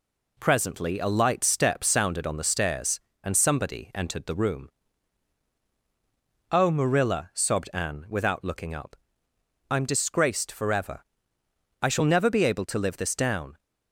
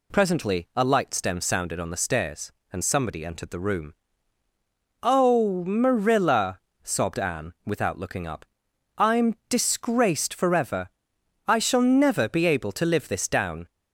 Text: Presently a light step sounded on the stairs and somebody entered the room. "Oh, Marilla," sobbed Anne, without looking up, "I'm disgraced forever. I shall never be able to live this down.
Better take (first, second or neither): first